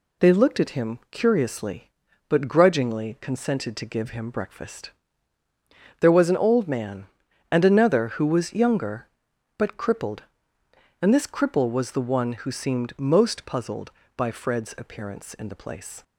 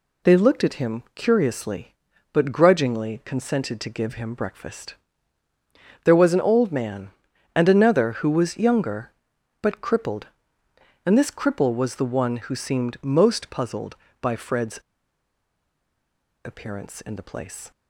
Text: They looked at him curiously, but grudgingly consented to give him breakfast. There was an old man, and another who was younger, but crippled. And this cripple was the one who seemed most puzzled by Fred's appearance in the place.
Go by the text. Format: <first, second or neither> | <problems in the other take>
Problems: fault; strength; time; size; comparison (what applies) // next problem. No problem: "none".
first | pauses between "Fred's" and "appearance"; strong; at 14.7 s; 1.6 s long